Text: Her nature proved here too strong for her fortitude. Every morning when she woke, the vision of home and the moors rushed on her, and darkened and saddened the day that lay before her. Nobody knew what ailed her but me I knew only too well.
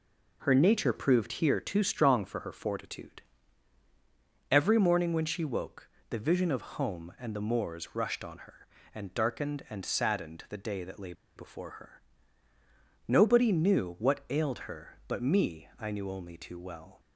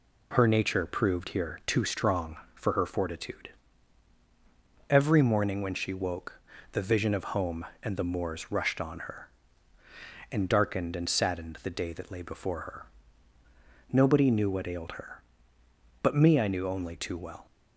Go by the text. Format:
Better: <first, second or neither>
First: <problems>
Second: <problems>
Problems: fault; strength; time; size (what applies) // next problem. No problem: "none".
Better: second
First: pauses between "lay" and "before"; slight; at 11.1 s; 0.23 s long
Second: none